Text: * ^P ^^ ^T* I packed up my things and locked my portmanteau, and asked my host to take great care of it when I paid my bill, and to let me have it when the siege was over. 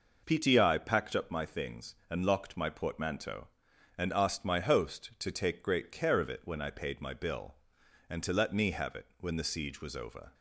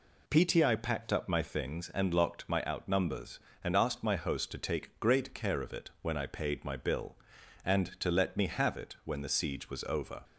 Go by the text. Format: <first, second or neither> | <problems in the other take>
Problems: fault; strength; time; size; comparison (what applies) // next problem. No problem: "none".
first | says "outnumbers" for "portmanteau"; at 2.6 s